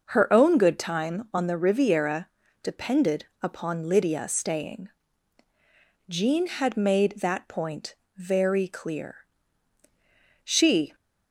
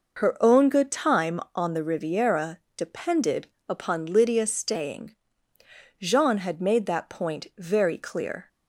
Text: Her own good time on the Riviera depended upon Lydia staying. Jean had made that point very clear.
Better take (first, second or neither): second